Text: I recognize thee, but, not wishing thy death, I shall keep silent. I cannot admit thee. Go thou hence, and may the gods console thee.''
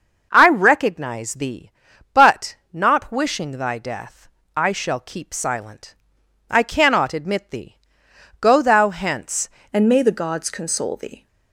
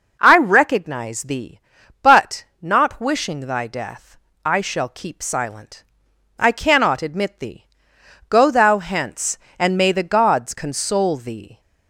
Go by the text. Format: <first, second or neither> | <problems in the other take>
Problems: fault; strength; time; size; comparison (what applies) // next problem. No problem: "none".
second | changes voice at "and"; from 9.7 s on; 1.5 s long